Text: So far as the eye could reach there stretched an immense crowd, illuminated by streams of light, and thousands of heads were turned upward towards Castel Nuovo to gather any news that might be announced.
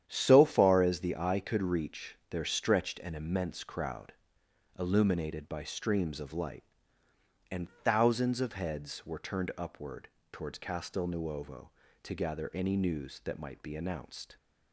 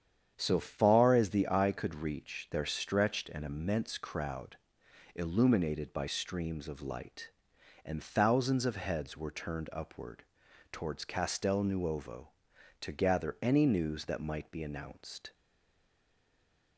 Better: first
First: starts louder than the rest; strong; until 1.0 s; 9.5 dB // pauses between "upward" and "towards"; slight; at 10.0 s; 0.22 s long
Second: starts louder than the rest; strong; until 1.3 s; 8.5 dB // pauses between "upward" and "towards"; noticeable; at 10.2 s; 0.48 s long // stays silent after the last word; noticeable; from 15.3 s on; 1.4 s long

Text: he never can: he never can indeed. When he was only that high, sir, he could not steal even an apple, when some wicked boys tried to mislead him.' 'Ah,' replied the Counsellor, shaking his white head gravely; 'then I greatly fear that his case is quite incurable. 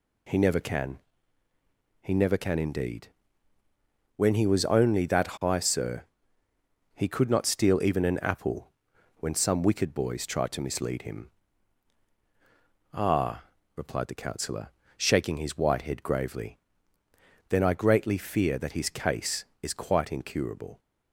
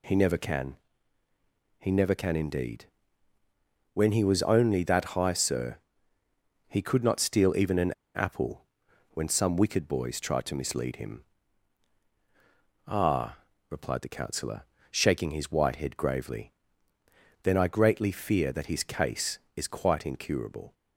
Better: first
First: none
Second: pauses between "an" and "apple"; slight; at 7.9 s; 0.23 s long

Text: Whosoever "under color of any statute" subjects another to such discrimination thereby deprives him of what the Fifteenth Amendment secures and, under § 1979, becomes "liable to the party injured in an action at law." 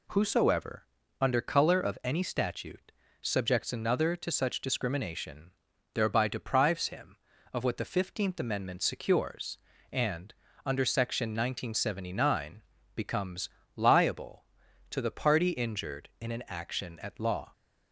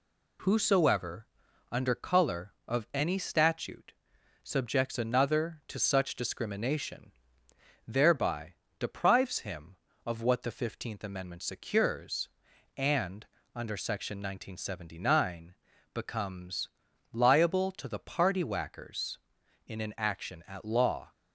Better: first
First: pauses between "Whosoever" and "under"; slight; at 0.8 s; 0.34 s long // pauses between "statute" and "subjects"; slight; at 2.9 s; 0.28 s long // pauses between "discrimination" and "thereby"; at 5.5 s; 0.40 s long // pauses between "becomes" and "liable"; slight; at 13.4 s; 0.26 s long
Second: pauses between "Whosoever" and "under"; at 1.2 s; 0.44 s long // pauses between "statute" and "subjects"; noticeable; at 3.9 s; 0.50 s long // pauses between "discrimination" and "thereby"; noticeable; at 7.1 s; 0.76 s long // pauses between "thereby" and "deprives"; slight; at 8.5 s; 0.24 s long // pauses between "becomes" and "liable"; at 16.6 s; 0.44 s long // says "whackers" for "injured"; at 18.4 s

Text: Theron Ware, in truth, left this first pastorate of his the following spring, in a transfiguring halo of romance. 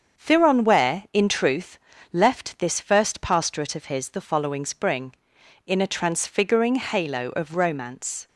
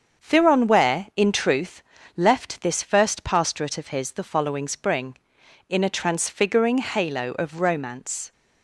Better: neither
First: starts louder than the rest; strong; until 1.2 s; 7 dB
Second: starts louder than the rest; strong; until 1.2 s; 7 dB

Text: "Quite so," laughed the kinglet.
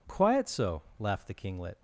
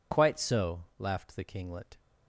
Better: second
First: says "Quiet" for "Quite"; at 0.0 s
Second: none

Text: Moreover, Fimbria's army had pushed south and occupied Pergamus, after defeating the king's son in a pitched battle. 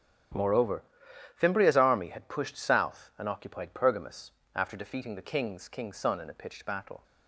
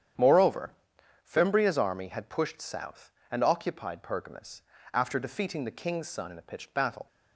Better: second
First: starts louder than the rest; strong; until 1.9 s; 11 dB // says "king's" twice; at 5.6 s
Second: starts louder than the rest; strong; until 1.7 s; 9 dB

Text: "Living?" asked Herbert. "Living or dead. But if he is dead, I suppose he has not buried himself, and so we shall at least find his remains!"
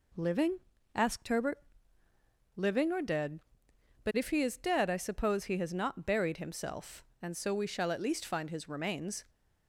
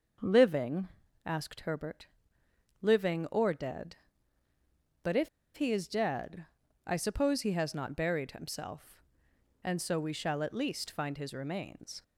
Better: first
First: none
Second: starts louder than the rest; noticeable; until 1.5 s; 6 dB // pauses between "if" and "he"; slight; at 5.2 s; 0.27 s long

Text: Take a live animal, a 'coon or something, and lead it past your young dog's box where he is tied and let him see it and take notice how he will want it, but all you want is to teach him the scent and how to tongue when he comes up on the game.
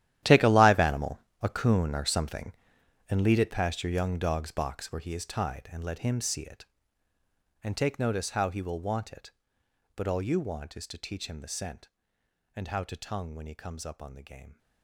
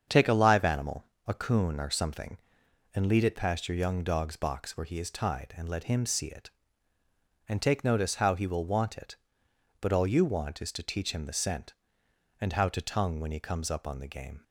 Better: second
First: gets quieter; strong; throughout; 16 dB // starts louder than the rest; strong; until 1.4 s; 12.5 dB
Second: starts louder than the rest; strong; until 1.3 s; 7.5 dB

